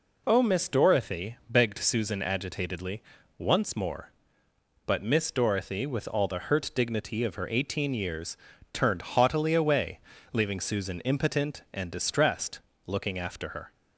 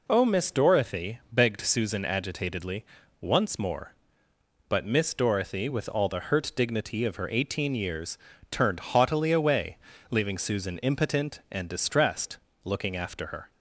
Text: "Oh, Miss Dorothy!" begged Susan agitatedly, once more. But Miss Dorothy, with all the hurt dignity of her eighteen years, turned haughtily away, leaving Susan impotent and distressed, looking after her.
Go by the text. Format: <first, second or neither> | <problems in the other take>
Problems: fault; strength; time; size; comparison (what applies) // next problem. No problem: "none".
neither | none